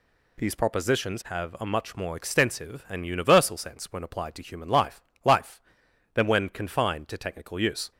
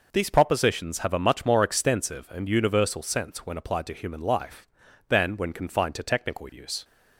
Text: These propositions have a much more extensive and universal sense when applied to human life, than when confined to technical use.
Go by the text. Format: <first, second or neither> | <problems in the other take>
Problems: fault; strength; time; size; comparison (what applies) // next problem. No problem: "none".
second | says "life" twice; at 5.2 s